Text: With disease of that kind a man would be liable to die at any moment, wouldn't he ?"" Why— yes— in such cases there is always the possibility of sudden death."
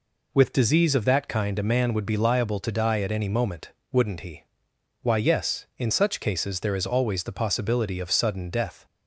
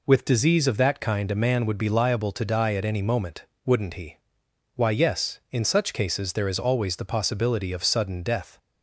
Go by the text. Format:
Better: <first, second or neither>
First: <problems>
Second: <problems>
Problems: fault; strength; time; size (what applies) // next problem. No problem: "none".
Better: neither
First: none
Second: none